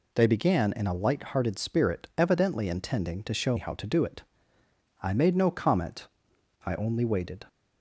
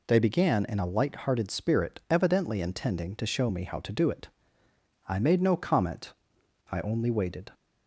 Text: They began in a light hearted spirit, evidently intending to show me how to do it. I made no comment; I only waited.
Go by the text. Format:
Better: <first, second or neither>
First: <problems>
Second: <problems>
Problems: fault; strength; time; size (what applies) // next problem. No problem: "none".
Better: second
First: skips "me"; at 3.5 s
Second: none